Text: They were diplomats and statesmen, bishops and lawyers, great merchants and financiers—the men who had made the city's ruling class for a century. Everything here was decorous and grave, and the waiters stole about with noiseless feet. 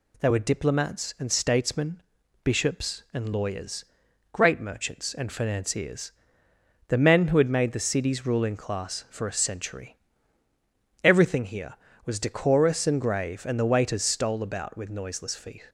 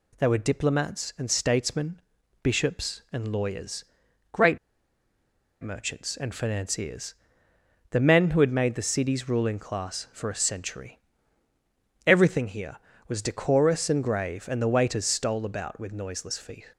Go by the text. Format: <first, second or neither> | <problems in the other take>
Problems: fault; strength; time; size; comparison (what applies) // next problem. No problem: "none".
first | pauses between "great" and "merchants"; at 4.5 s; 1.0 s long